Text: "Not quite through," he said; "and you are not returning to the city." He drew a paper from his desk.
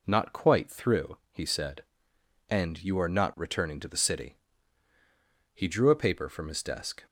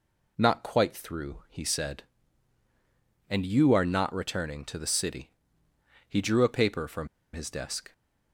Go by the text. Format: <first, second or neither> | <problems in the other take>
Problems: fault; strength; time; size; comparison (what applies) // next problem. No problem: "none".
first | pauses between "from" and "his"; slight; at 7.0 s; 0.26 s long